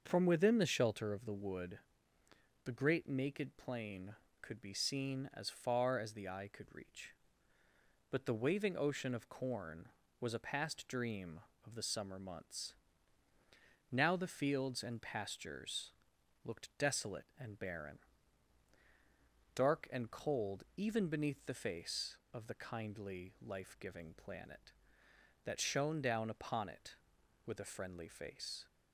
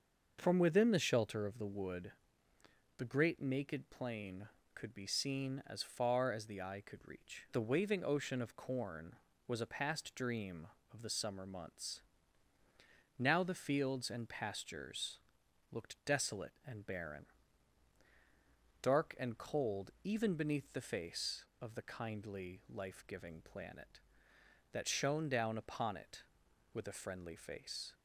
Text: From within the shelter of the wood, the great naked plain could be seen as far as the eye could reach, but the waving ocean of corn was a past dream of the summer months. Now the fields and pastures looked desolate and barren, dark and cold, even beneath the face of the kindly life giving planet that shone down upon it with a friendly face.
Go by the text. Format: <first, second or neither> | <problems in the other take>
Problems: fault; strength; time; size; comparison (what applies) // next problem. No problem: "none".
first | starts louder than the rest; until 1.4 s; 6 dB; also in the first // skips "but"; at 7.4 s // pauses between "pastures" and "looked"; noticeable; at 15.1 s; 0.54 s long; noticeable in the first